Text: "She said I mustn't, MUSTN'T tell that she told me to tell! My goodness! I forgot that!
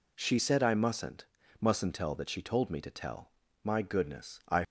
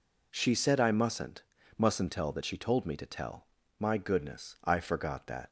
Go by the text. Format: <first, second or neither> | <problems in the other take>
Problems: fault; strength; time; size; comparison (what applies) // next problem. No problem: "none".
second | stops before "forgot that"; at 4.6 s